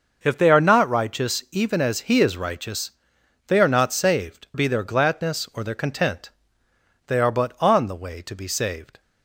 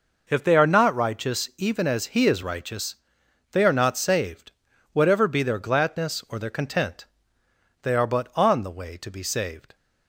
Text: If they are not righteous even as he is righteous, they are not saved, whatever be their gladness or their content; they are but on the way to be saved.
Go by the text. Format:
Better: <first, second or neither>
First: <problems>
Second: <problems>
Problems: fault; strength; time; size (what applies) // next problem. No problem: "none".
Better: second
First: starts louder than the rest; noticeable; until 1.2 s; 6 dB // skips "whatever"; at 4.5 s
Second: none